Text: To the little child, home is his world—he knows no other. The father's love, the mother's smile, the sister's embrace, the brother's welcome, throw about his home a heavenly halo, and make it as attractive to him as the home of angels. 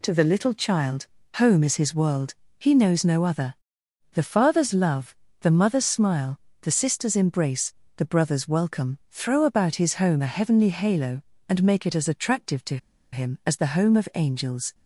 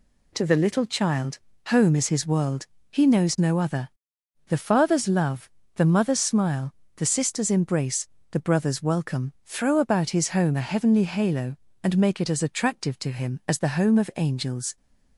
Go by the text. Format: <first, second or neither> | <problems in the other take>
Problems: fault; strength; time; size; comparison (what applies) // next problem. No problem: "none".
second | pauses between "to" and "him"; slight; at 12.7 s; 0.35 s long